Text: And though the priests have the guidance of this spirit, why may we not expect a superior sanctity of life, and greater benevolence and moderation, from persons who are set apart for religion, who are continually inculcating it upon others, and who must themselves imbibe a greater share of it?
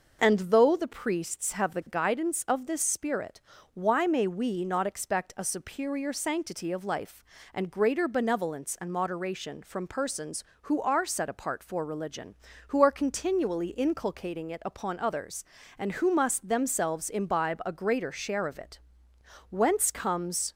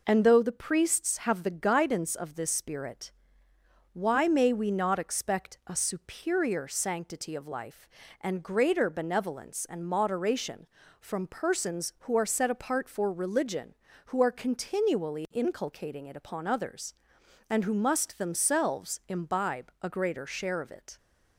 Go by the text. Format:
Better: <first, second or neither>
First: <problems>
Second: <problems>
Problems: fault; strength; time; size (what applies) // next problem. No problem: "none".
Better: second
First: goes on to say "Whence comes"; noticeable; from 19.4 s on; 1.0 s long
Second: none